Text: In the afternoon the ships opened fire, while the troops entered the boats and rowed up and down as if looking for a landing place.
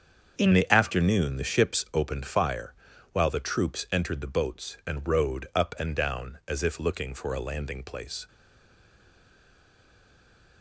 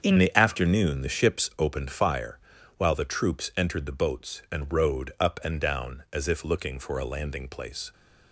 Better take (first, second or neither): second